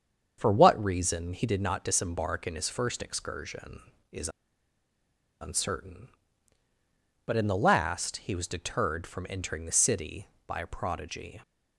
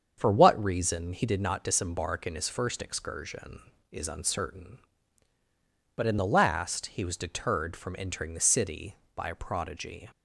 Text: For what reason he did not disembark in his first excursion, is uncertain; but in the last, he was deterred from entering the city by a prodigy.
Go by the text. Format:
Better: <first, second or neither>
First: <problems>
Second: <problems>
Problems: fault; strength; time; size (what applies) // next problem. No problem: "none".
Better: second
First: starts louder than the rest; strong; until 1.4 s; 7.5 dB // pauses between "is" and "uncertain"; at 4.2 s; 1.1 s long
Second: starts louder than the rest; strong; until 1.1 s; 7.5 dB